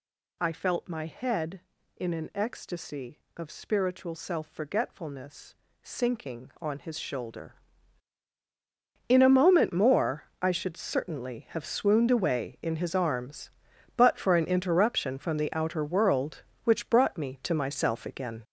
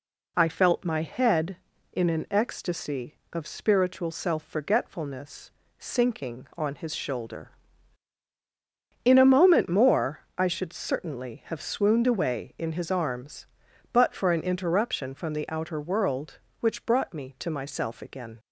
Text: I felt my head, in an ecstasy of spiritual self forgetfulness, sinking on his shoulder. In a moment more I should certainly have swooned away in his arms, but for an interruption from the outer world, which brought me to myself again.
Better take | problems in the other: second | gets louder; strong; throughout; 7 dB // pauses between "more" and "I"; slight; at 10.2 s; 0.18 s long; slight in the second

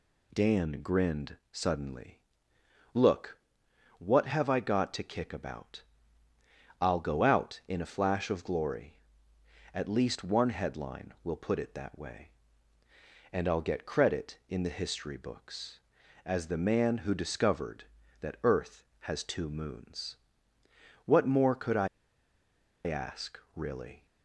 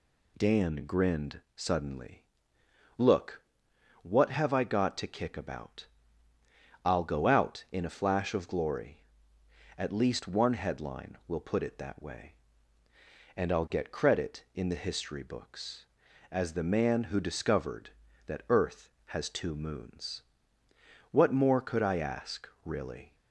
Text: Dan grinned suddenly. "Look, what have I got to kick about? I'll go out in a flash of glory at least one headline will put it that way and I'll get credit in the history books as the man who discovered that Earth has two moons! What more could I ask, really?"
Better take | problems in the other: second | pauses between "I" and "ask"; at 21.8 s; 0.99 s long

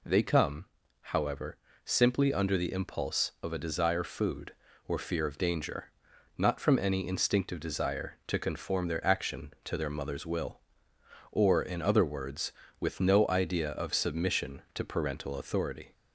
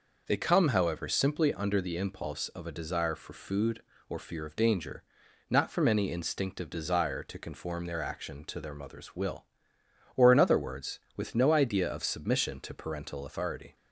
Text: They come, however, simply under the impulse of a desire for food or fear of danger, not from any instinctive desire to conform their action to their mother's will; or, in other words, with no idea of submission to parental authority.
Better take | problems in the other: second | skips "for"; at 4.0 s

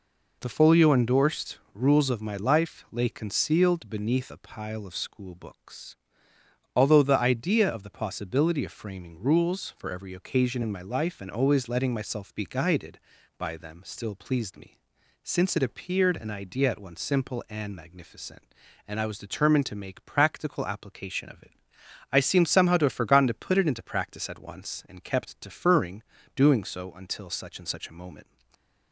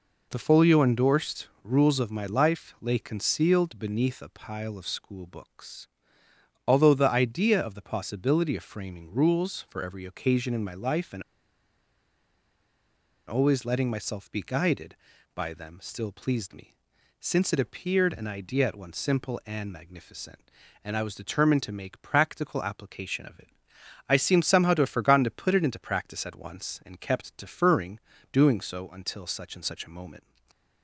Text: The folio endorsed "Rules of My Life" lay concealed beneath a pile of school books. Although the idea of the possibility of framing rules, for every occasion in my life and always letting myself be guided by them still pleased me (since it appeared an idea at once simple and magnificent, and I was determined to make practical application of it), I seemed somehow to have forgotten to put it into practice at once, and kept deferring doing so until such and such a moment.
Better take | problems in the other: first | pauses between "endorsed" and "Rules"; slight; at 1.4 s; 0.16 s long; slight in the first // pauses between "and" and "always"; strong; at 11.2 s; 2.0 s long // pauses between "deferring" and "doing"; slight; at 27.9 s; 0.34 s long; slight in the first // stays silent after the last word; slight; from 30.1 s on; 0.7 s long

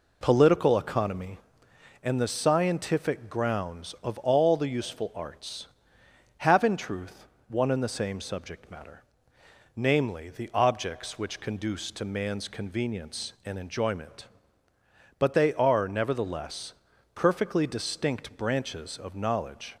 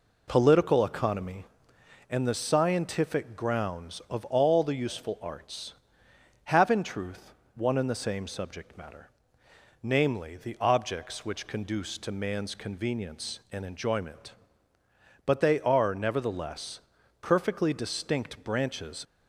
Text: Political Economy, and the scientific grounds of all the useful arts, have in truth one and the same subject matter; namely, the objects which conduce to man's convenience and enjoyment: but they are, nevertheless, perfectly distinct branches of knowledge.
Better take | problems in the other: first | pauses between "truth" and "one"; slight; at 7.3 s; 0.22 s long; slight in the first // stops before "of knowledge"; at 19.0 s

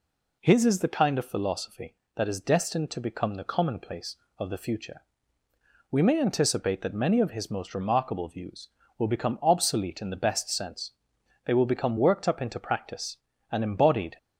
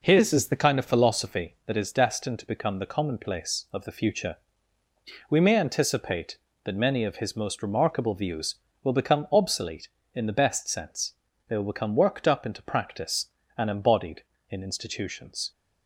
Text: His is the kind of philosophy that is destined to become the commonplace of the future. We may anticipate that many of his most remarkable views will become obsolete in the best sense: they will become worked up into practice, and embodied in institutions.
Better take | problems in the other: second | stops before "in institutions"; at 14.1 s

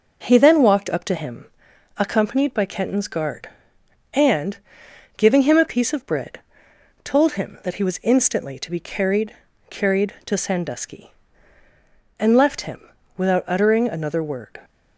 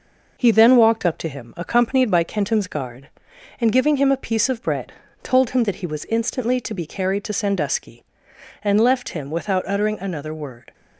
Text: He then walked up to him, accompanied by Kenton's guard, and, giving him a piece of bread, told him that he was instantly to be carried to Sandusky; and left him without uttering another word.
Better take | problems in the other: second | says "carried" twice; at 9.6 s // pauses between "him" and "without"; slight; at 12.8 s; 0.36 s long

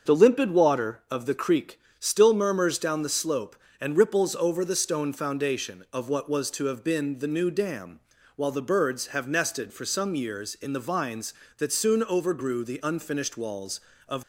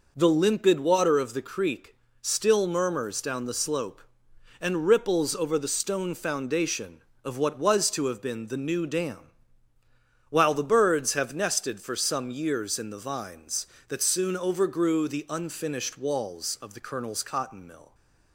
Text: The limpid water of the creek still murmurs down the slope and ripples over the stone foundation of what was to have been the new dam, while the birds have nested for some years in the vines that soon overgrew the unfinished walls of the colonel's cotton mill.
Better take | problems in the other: second | starts louder than the rest; until 1.1 s; 6.5 dB // pauses between "creek" and "still"; slight; at 1.8 s; 0.18 s long; slight in the second // stops before "the colonel's cotton mill"; at 14.2 s

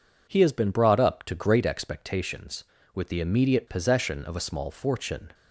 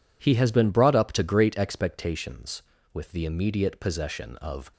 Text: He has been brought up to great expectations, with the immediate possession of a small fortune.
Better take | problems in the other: first | stops before "a small fortune"; at 4.7 s

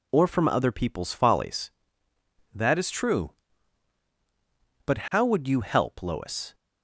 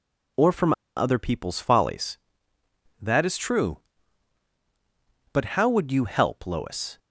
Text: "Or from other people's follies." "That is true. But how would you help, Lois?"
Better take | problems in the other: first | pauses between "from" and "other"; slight; at 0.7 s; 0.24 s long

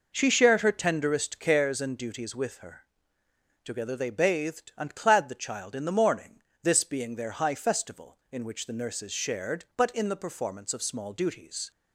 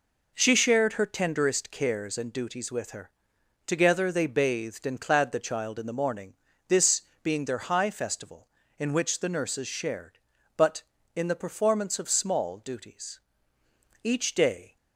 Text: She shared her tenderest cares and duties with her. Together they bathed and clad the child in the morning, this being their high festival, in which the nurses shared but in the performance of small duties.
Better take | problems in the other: first | pauses between "this" and "being"; slight; at 7.0 s; 0.20 s long // goes on to say "Each day"; noticeable; from 14.0 s on; 0.72 s long

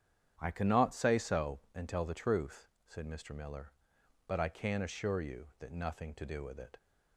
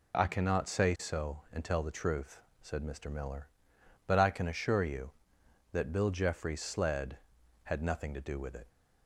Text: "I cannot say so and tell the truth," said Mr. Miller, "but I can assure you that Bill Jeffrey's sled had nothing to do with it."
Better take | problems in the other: second | starts louder than the rest; strong; until 1.4 s; 9 dB // skips "Bill Jeffrey's sled had"; at 5.7 s

